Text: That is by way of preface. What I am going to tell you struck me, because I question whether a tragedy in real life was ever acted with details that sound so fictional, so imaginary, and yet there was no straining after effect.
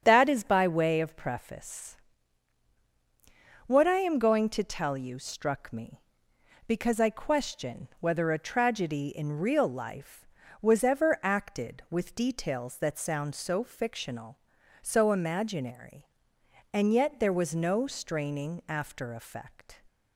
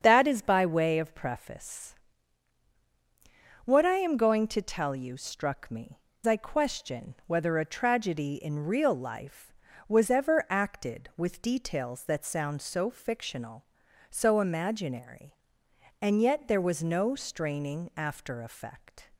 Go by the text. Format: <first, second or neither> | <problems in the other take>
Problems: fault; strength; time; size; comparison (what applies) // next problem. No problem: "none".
first | starts louder than the rest; strong; until 1.0 s; 7.5 dB; strong in the first // skips "because"; at 6.1 s